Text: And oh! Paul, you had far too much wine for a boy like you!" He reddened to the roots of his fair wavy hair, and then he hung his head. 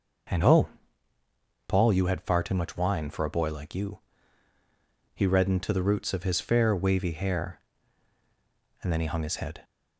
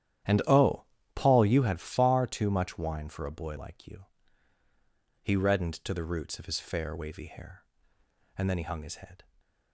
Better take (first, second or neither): first